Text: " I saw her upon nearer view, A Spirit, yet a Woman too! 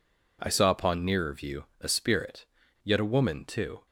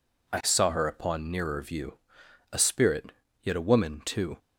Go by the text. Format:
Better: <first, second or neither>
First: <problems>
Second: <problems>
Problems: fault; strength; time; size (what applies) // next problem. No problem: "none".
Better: second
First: skips "her"; at 0.6 s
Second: none